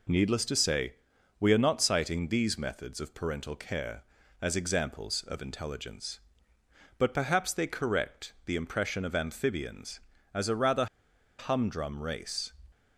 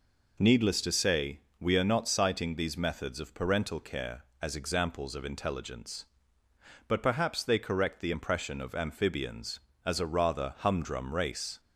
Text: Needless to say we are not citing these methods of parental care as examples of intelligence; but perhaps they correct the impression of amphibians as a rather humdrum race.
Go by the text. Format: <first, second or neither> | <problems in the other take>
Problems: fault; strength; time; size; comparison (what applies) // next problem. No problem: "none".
second | pauses between "say" and "we"; at 0.9 s; 0.44 s long; slight in the second // pauses between "rather" and "humdrum"; noticeable; at 10.8 s; 0.52 s long